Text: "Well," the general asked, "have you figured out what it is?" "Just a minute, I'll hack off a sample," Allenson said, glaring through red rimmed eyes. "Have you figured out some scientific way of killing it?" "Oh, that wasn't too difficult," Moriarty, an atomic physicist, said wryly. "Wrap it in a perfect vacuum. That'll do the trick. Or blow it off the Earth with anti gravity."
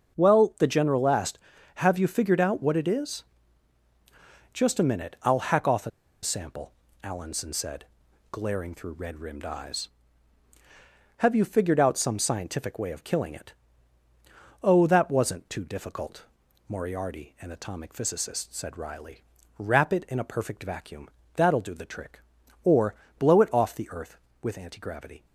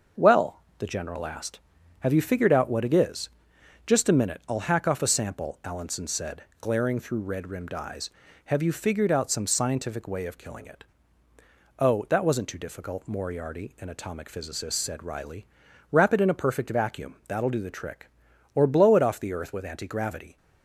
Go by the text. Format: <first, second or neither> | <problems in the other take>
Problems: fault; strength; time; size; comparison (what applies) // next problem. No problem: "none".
second | starts louder than the rest; until 1.1 s; 6.5 dB; also in the second // pauses between "a" and "sample"; slight; at 5.9 s; 0.32 s long // pauses between "Or" and "blow"; slight; at 22.9 s; 0.24 s long